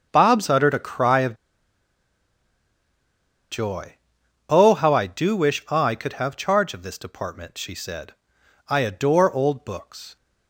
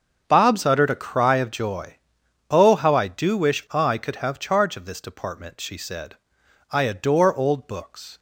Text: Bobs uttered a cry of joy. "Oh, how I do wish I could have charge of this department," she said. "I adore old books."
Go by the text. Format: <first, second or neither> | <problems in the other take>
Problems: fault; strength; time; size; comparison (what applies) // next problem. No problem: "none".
second | starts louder than the rest; until 1.1 s; 7 dB; also in the second // pauses between "of" and "joy"; strong; at 1.3 s; 2.1 s long